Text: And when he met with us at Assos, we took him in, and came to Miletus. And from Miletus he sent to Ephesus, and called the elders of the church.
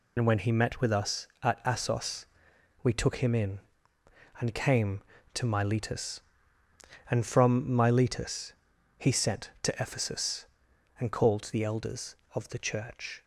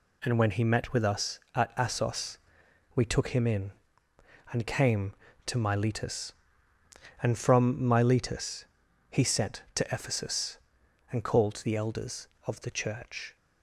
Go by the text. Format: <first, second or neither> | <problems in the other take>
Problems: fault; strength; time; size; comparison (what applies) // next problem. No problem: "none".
second | loses the start of "And"; at 0.1 s; 75 ms // pauses between "Miletus" and "he"; at 8.5 s; 0.44 s long; also in the second